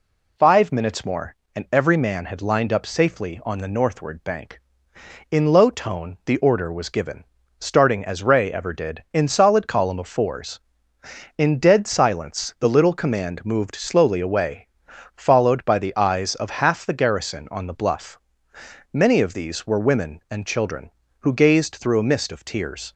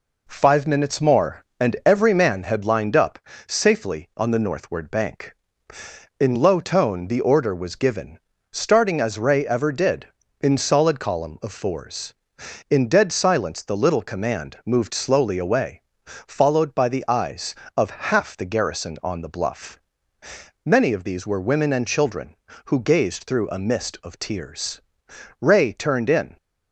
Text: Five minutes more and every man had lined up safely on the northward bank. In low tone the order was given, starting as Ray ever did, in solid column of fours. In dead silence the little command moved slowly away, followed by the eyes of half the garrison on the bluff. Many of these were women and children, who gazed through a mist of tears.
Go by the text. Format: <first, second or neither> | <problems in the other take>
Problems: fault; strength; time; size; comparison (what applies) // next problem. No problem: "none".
first | pauses between "up" and "safely"; slight; at 3.1 s; 0.30 s long // goes on to say "Ray turned in"; noticeable; from 25.4 s on; 0.96 s long